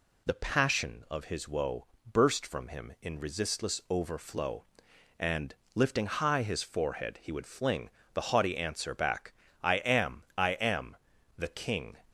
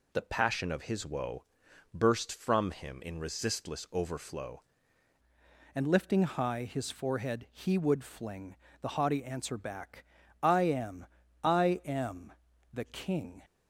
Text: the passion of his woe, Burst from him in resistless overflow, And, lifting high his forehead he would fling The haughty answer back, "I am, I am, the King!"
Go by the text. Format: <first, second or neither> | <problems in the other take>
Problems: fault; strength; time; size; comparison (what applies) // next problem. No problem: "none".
first | changes voice at "And"; from 5.7 s on; 7.7 s long // pauses between "fling" and "The"; slight; at 8.5 s; 0.24 s long; slight in the first